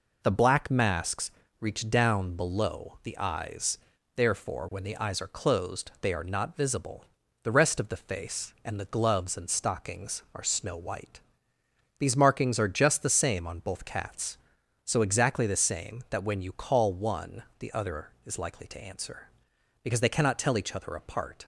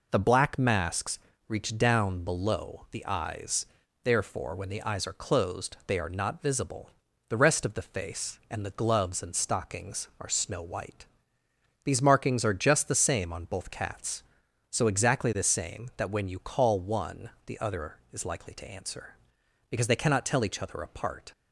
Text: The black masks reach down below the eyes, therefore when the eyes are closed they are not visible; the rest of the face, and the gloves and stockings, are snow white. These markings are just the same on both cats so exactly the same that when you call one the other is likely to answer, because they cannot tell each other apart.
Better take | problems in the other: neither | pauses between "masks" and "reach"; slight; the same in both // pauses between "one" and "the"; slight; the same in both

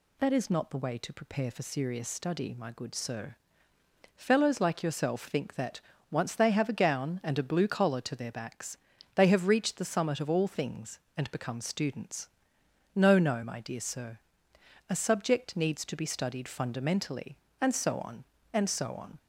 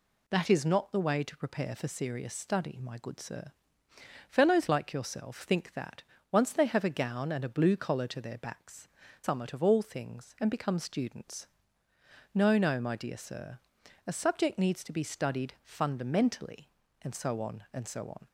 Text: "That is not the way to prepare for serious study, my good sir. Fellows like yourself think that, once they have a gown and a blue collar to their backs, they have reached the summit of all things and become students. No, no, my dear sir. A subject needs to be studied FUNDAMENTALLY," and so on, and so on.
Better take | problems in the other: first | skips "they have reached the"; at 9.0 s

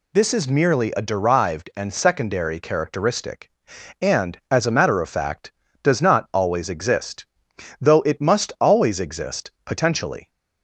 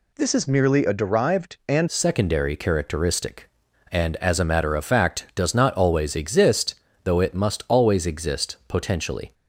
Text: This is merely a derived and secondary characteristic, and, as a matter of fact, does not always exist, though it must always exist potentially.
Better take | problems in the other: first | changes voice at "secondary"; from 1.8 s on; 7.5 s long

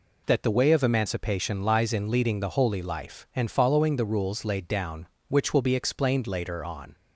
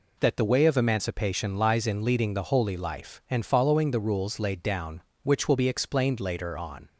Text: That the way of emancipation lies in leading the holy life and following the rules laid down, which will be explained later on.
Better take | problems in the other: neither | none

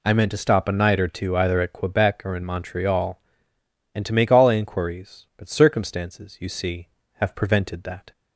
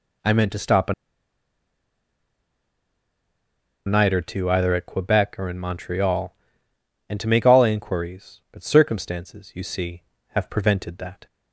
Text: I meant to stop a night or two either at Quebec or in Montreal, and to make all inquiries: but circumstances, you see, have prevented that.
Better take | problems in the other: first | pauses between "a" and "night"; strong; at 0.9 s; 2.9 s long

